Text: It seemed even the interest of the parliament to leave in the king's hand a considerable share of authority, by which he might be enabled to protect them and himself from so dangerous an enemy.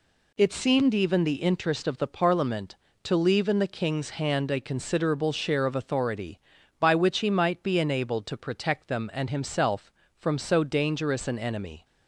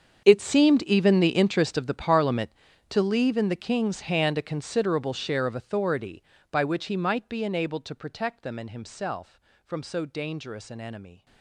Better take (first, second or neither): first